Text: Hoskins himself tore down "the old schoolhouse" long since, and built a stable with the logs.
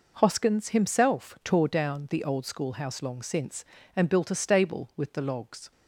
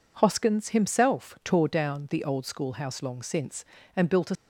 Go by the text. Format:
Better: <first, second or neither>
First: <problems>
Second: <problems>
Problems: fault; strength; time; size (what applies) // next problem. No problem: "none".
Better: first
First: none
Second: stops before "stable with the logs"; at 4.3 s